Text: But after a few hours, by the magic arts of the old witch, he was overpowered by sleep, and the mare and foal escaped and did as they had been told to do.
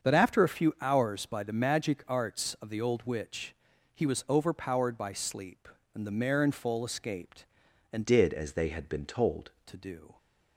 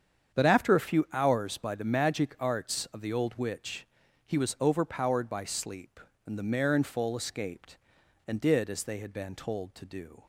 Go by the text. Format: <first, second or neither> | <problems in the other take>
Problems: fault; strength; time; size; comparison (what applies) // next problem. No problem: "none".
second | starts louder than the rest; until 1.1 s; 7 dB; strong in the second // changes voice from "did" to "told"; from 8.0 to 9.5 s; 1.5 s long